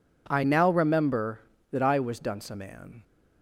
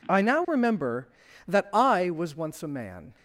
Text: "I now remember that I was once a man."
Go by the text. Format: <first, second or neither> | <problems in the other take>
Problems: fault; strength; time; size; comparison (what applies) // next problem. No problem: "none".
second | says "dunce" for "once"; at 2.1 s